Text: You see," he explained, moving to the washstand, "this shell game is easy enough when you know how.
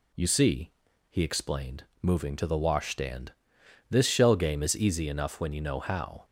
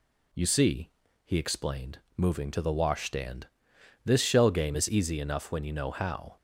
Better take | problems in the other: neither | none

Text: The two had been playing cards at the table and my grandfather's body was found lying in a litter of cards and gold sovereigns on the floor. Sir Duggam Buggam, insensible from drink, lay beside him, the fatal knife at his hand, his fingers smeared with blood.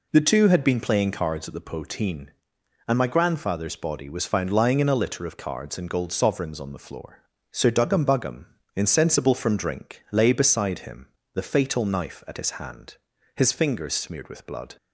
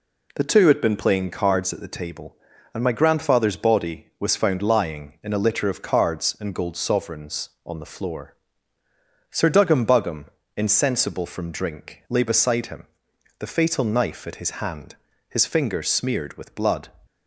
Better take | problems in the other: second | says "poteen" for "table"; at 1.6 s

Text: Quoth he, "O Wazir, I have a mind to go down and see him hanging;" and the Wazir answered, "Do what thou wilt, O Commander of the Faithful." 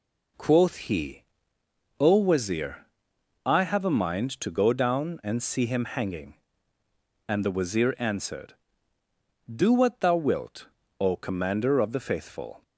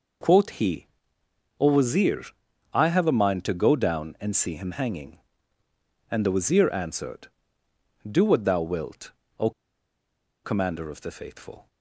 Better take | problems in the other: first | pauses between "O" and "Commander"; noticeable; at 9.5 s; 0.94 s long

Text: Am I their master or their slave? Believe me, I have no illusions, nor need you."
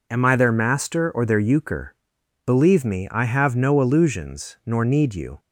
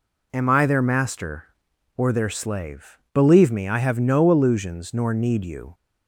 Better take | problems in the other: second | says "euchre" for "slave"; at 1.3 s

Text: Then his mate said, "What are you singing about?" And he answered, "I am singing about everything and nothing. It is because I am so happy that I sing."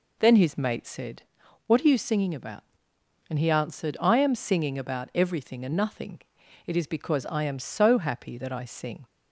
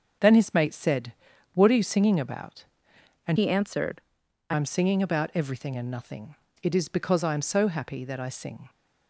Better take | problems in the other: first | starts louder than the rest; until 1.6 s; 7 dB // changes voice from "he" to "I"; from 3.3 to 4.5 s; 1.2 s long

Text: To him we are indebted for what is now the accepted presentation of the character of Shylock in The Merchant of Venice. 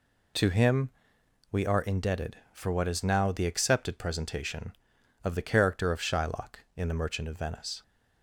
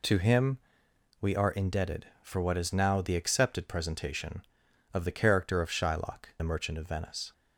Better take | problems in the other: first | pauses between "him" and "we"; noticeable; at 0.5 s; 0.62 s long; noticeable in the first // skips "in"; at 6.3 s

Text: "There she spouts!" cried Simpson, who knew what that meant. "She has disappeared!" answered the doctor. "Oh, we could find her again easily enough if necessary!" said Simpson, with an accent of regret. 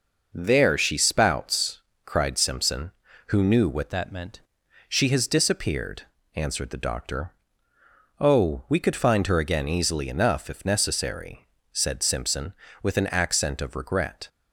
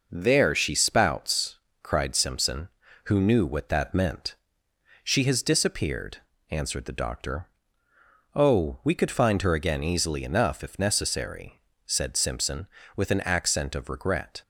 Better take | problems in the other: second | changes voice from "that" to "meant"; from 3.9 to 4.4 s; 0.5 s long

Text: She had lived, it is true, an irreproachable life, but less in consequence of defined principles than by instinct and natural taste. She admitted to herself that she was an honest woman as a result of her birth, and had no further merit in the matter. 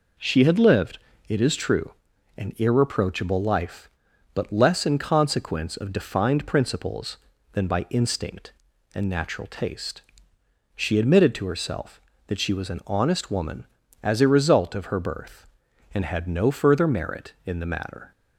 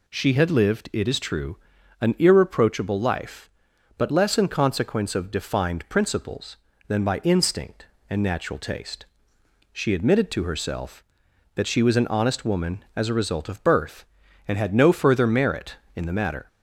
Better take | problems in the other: first | skips "her"; at 13.6 s

